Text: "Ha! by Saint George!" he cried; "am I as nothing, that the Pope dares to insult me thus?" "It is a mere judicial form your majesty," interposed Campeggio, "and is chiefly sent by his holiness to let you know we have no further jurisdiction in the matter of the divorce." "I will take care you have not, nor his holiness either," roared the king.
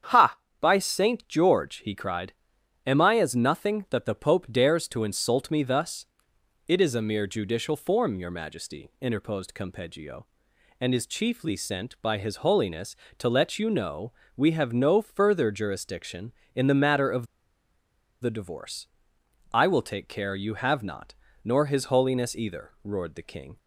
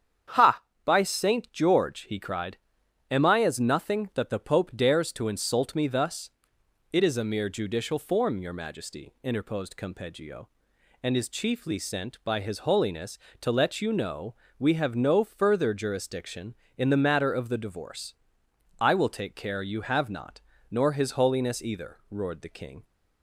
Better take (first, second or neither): second